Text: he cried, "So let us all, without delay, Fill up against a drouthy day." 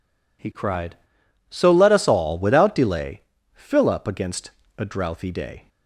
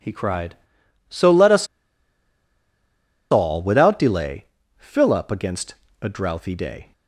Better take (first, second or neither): first